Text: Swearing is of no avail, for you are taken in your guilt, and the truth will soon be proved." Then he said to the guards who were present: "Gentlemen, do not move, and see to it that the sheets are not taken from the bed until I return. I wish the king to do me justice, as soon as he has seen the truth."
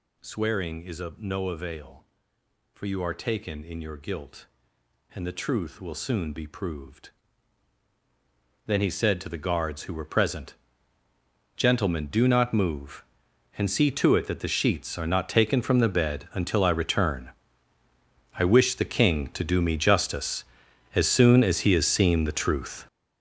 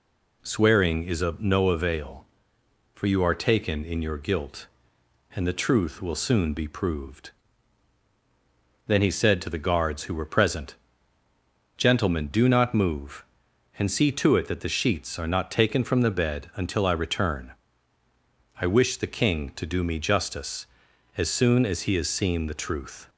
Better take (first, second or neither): second